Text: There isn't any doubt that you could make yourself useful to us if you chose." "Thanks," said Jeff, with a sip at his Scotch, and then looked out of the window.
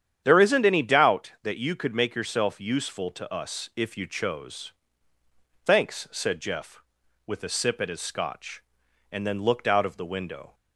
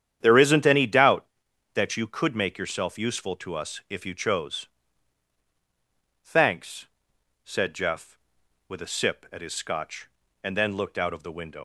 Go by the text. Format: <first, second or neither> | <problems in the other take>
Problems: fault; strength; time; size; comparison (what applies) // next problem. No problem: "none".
first | starts louder than the rest; strong; until 1.2 s; 9.5 dB; strong in the first // leaves "window" unfinished; at 11.5 s; 95 ms